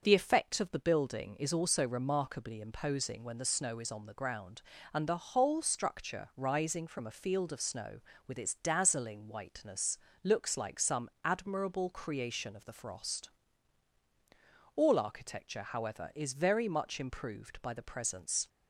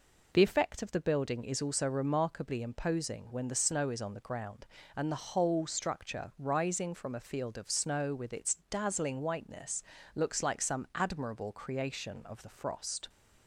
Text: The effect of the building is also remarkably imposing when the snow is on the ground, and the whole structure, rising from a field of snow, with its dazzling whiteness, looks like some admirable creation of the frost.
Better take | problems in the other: second | starts louder than the rest; until 1.0 s; 6 dB // pauses between "some" and "admirable"; slight; at 11.0 s; 0.16 s long // goes on to say "All architecture however is very much improved by the presence"; strong; from 14.7 s on; 3.7 s long

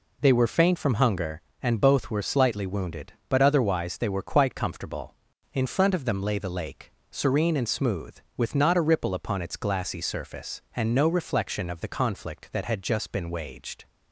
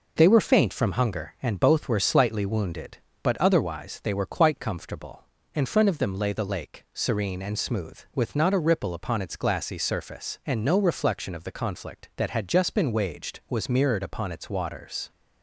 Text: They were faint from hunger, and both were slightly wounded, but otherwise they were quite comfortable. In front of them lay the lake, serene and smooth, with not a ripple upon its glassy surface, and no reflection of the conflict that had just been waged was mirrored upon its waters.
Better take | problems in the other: second | stops before "was mirrored upon its waters"; at 13.8 s

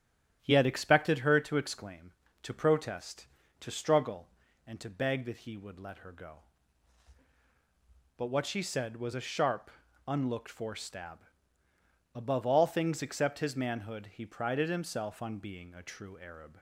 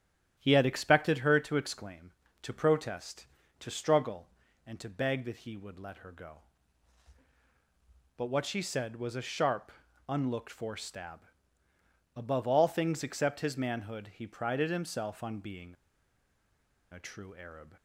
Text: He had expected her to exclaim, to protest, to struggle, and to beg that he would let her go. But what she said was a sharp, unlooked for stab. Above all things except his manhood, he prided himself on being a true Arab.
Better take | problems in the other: first | starts louder than the rest; strong; until 1.3 s; 10.5 dB; strong in the first // pauses between "being" and "a"; at 15.7 s; 1.1 s long

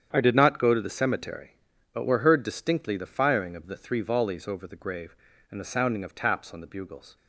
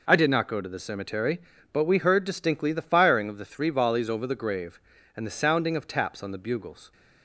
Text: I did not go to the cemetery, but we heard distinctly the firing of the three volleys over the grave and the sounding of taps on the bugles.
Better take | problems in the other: second | starts louder than the rest; strong; until 1.1 s; 8.5 dB // says "were" for "we"; at 2.0 s

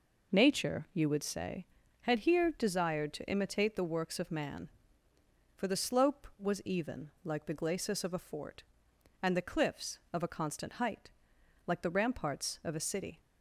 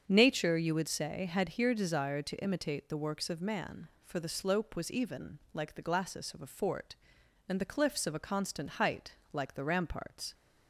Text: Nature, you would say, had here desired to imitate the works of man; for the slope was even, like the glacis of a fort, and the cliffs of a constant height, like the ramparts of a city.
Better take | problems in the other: first | starts louder than the rest; until 1.0 s; 7 dB // stops before "of a city"; at 10.3 s

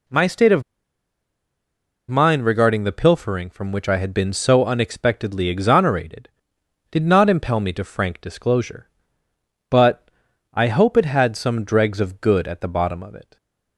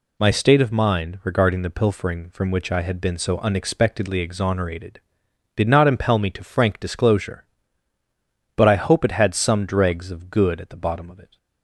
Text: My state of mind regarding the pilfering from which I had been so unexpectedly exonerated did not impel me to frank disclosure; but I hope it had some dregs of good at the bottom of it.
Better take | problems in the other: second | pauses between "of" and "mind"; strong; at 0.6 s; 1.4 s long // pauses between "but" and "I"; noticeable; at 10.0 s; 0.46 s long

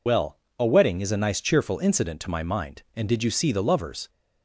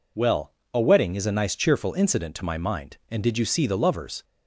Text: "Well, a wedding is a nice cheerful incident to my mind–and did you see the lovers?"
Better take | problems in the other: second | loses the start of "Well"; at 0.0 s; 50 ms

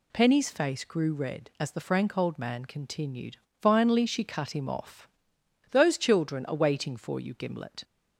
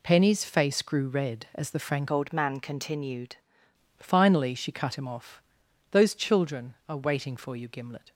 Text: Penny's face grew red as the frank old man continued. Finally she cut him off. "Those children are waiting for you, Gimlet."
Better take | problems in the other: first | changes voice from "old" to "continued"; from 2.1 to 3.3 s; 1.2 s long

